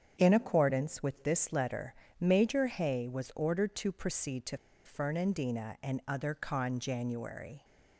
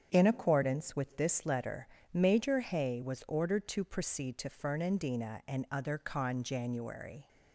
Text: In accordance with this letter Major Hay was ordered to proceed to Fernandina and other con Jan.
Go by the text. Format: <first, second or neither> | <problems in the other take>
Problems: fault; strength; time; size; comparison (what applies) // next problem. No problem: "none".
second | starts louder than the rest; strong; until 1.1 s; 8 dB; strong in the second // pauses between "letter" and "Major"; slight; at 1.9 s; 0.26 s long; slight in the second // pauses between "to" and "Fernandina"; slight; at 4.5 s; 0.28 s long